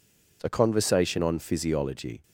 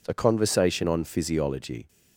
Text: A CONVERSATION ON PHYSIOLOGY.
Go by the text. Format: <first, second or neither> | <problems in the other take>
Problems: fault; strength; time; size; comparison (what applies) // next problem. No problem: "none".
neither | none